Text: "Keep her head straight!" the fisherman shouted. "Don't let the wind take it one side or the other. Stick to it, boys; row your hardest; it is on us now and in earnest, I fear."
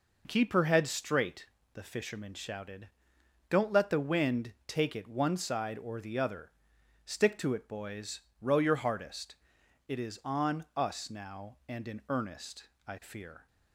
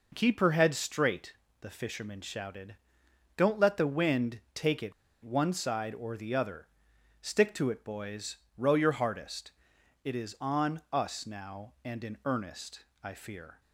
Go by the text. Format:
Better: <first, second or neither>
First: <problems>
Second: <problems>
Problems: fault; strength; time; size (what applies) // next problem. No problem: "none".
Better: first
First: none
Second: pauses between "it" and "one"; slight; at 4.9 s; 0.29 s long